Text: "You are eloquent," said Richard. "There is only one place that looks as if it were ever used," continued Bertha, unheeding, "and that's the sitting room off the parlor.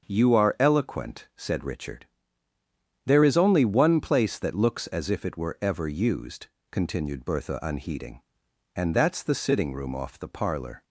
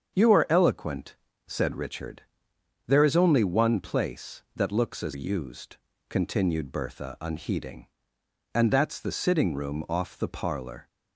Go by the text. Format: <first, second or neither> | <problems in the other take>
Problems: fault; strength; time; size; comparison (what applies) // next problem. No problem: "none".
first | starts louder than the rest; until 1.5 s; 7 dB; also in the first // skips "if it were ever"; at 5.1 s